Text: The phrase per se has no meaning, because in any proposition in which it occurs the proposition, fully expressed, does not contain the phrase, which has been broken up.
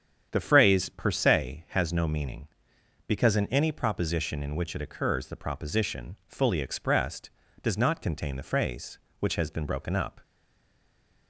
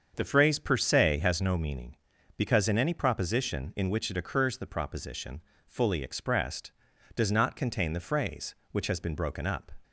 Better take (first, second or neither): second